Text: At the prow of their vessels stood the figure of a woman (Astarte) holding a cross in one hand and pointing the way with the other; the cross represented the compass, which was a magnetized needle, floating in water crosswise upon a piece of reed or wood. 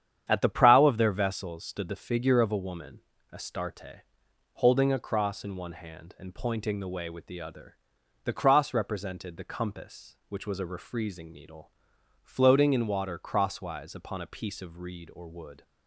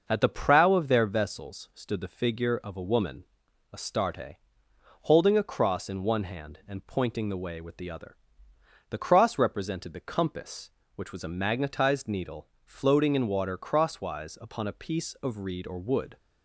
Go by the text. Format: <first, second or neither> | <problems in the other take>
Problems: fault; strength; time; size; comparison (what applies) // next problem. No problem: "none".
second | starts louder than the rest; strong; until 1.2 s; 9 dB; noticeable in the second // says "refreezing" for "magnetized"; at 10.6 s